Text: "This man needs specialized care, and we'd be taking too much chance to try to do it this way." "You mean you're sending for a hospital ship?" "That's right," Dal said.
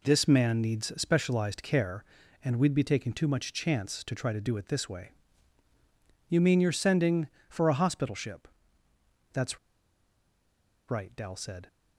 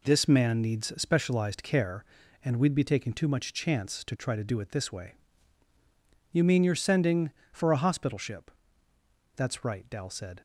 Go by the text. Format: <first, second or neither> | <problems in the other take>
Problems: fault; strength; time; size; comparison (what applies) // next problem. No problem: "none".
second | pauses between "That's" and "right"; strong; at 9.5 s; 1.3 s long